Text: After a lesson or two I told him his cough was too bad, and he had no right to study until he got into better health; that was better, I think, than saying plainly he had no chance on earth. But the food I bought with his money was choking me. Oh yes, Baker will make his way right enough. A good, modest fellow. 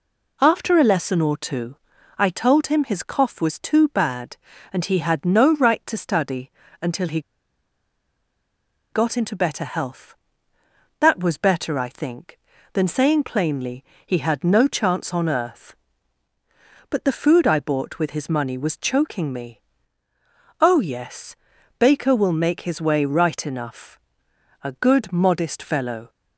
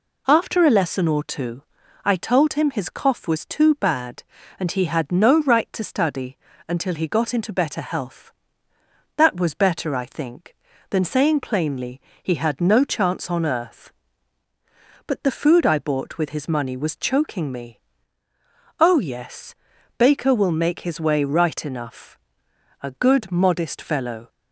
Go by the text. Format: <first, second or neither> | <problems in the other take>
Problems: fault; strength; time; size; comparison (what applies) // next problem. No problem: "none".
second | pauses between "two" and "I"; at 1.7 s; 0.40 s long; also in the second // pauses between "study" and "until"; slight; at 6.5 s; 0.30 s long; slight in the second // pauses between "he" and "got"; strong; at 7.1 s; 1.7 s long // pauses between "plainly" and "he"; slight; at 13.8 s; 0.22 s long; slight in the second